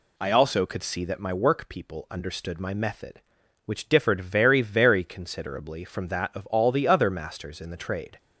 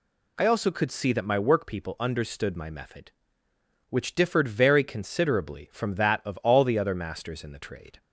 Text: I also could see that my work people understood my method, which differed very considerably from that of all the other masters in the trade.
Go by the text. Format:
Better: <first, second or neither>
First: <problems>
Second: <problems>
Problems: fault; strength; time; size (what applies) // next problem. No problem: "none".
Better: second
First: says "very" twice; at 4.6 s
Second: none